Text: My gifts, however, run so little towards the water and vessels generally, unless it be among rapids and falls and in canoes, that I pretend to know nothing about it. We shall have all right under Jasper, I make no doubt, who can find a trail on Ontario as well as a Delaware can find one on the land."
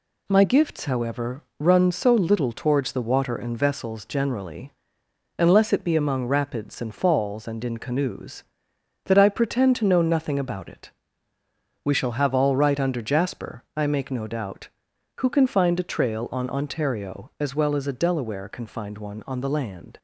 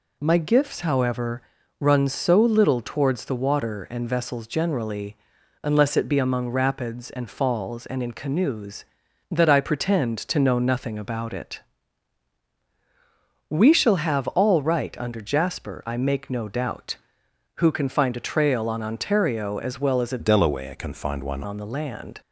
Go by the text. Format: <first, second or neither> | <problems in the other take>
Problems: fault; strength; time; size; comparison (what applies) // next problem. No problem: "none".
first | changes voice from "Delaware" to "one"; from 20.1 to 21.4 s; 1.3 s long